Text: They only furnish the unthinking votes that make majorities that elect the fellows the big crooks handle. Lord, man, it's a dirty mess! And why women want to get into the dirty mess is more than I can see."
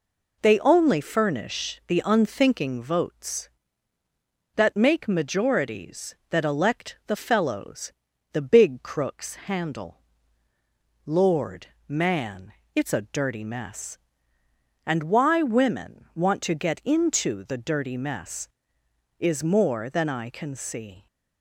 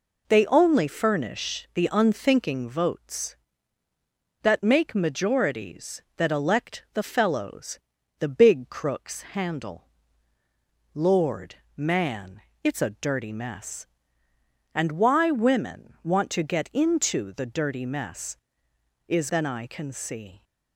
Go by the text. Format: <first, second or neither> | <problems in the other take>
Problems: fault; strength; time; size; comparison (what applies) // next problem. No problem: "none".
first | pauses between "fellows" and "the"; at 7.7 s; 0.40 s long; also in the first // skips "more"; at 19.2 s